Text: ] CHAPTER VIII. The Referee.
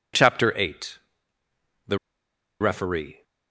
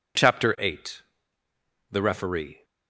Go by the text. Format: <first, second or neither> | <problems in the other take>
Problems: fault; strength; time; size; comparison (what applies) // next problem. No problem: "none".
second | pauses between "The" and "Referee"; noticeable; at 1.9 s; 0.63 s long